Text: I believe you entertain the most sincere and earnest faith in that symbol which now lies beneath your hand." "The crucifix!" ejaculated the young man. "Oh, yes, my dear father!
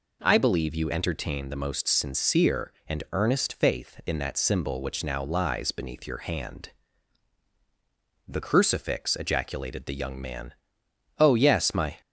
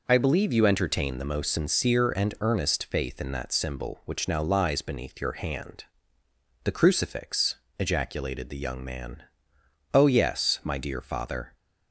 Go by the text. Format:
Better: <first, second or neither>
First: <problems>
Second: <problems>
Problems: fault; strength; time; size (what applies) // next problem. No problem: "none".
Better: second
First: stops before "dear father"; at 12.0 s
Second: none